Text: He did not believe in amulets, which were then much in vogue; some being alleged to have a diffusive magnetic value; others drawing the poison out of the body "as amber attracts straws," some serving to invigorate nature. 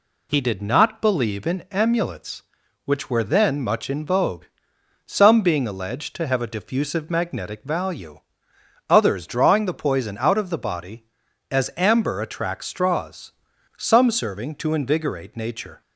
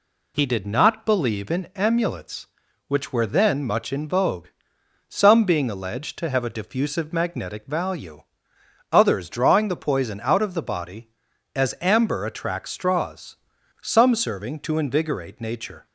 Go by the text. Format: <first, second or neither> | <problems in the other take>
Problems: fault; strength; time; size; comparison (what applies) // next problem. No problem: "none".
neither | none